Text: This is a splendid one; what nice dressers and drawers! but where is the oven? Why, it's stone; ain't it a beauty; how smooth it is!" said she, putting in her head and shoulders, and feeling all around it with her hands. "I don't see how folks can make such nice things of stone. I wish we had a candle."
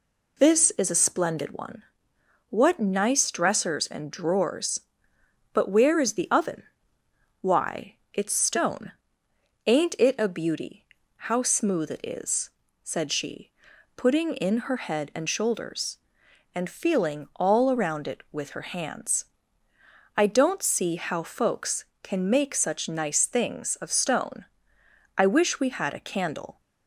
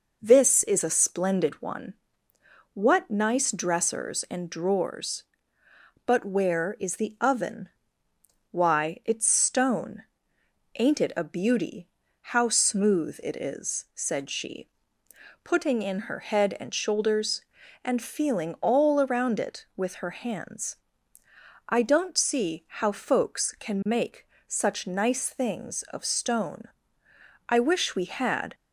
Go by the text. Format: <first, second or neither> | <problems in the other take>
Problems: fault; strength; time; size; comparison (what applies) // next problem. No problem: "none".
first | pauses between "make" and "such"; slight; at 24.2 s; 0.22 s long // stops before "a candle"; at 28.5 s